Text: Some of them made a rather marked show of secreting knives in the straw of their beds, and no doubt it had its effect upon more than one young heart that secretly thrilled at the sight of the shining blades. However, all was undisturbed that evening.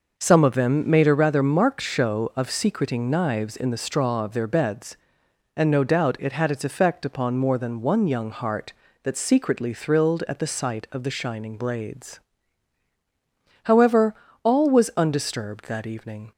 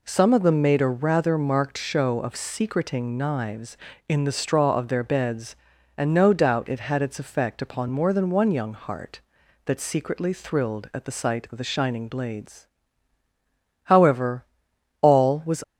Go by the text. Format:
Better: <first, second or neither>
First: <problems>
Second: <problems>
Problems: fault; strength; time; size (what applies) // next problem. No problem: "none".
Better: first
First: none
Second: stops before "undisturbed that evening"; at 15.6 s